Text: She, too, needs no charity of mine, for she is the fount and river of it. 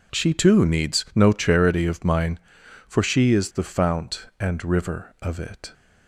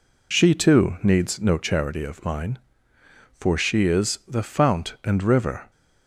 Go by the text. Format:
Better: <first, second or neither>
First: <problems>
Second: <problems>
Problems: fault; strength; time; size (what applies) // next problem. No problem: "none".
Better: first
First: none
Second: stops before "of it"; at 5.7 s